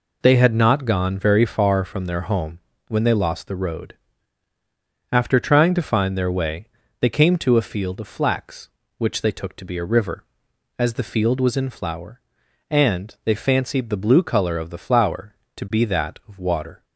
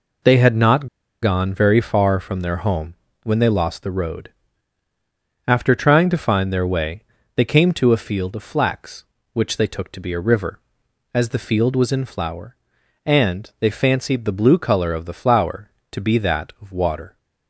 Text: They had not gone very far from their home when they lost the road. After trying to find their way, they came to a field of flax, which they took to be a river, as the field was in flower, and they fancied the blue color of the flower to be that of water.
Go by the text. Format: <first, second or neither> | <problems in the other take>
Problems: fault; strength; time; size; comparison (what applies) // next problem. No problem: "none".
first | pauses between "not" and "gone"; slight; at 0.8 s; 0.35 s long // pauses between "home" and "when"; slight; at 2.9 s; 0.26 s long; slight in the first